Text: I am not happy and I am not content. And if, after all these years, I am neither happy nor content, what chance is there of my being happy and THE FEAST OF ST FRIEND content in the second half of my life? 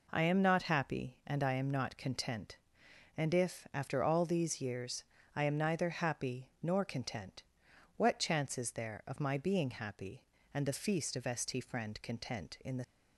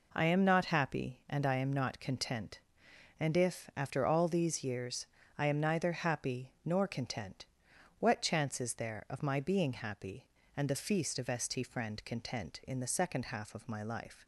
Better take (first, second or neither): second